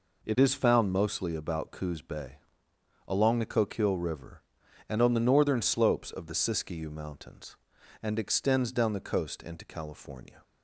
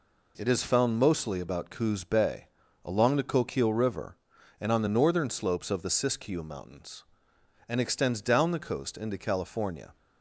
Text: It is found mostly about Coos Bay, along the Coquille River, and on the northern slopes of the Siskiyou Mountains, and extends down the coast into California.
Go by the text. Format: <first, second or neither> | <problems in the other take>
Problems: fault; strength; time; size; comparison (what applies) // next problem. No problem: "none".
neither | none